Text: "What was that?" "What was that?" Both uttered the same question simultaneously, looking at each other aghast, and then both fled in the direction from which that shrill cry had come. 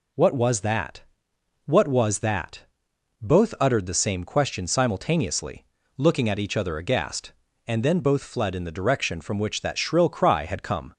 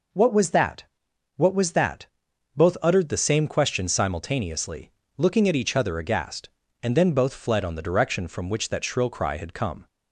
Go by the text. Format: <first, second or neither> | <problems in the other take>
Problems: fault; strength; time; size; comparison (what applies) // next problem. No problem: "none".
first | says "on" for "in"; at 7.6 s